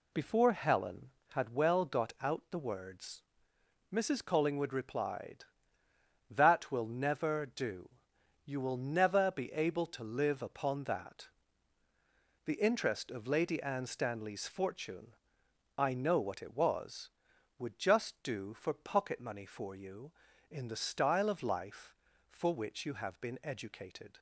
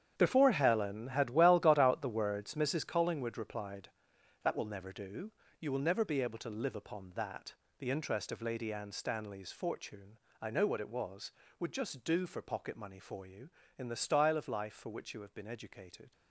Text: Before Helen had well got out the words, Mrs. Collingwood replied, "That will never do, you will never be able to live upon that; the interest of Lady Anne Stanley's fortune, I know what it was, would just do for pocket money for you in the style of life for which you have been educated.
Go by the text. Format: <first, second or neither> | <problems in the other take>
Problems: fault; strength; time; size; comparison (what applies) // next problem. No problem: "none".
first | gets quieter; strong; throughout; 13 dB